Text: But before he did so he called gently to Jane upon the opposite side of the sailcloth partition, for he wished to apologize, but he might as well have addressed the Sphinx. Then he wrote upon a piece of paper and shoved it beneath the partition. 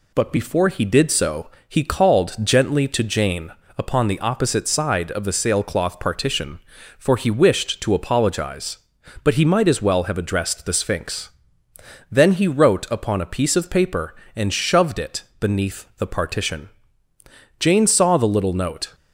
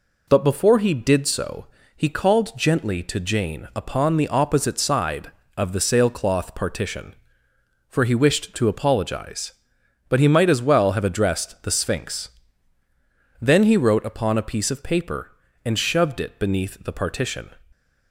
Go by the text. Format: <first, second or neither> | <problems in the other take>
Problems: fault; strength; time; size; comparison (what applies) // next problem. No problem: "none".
second | pauses between "so" and "he"; slight; at 1.4 s; 0.18 s long; slight in the second // pauses between "Jane" and "upon"; slight; at 3.5 s; 0.28 s long // pauses between "it" and "beneath"; slight; at 15.2 s; 0.18 s long // goes on to say "Jane saw the little note"; from 17.5 s on; 1.3 s long